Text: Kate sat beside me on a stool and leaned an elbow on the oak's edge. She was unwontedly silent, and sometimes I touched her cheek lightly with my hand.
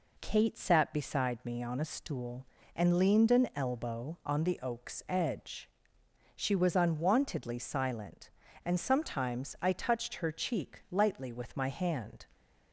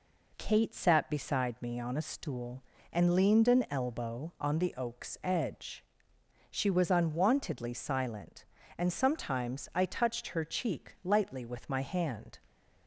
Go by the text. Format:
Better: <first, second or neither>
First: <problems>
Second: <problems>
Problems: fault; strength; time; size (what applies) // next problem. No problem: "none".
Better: neither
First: none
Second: none